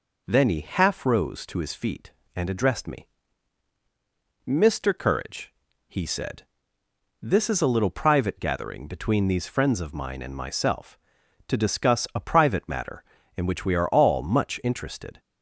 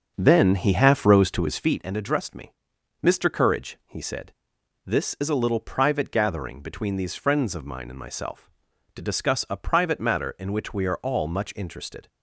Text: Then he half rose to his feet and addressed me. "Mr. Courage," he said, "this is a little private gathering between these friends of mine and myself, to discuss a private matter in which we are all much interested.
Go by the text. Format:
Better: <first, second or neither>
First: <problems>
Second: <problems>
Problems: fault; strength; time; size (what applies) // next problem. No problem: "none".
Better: first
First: none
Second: starts louder than the rest; until 1.8 s; 6.5 dB